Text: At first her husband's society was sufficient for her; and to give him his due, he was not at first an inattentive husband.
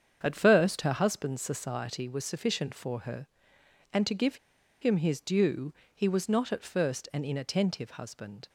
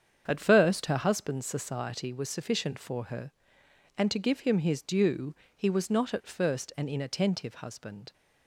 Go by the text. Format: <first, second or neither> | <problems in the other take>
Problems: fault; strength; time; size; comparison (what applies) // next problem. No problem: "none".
second | starts louder than the rest; strong; until 1.2 s; 7.5 dB; strong in the second // pauses between "give" and "him"; at 4.3 s; 0.45 s long